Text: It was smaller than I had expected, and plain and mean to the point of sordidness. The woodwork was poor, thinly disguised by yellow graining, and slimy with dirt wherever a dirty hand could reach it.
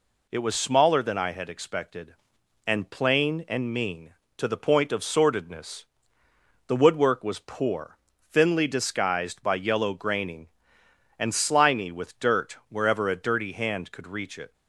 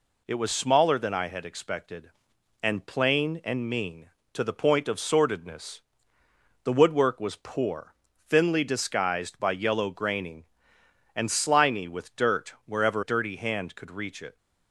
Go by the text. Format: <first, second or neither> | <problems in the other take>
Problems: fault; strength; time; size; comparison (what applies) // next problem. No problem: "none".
first | skips "a"; at 13.0 s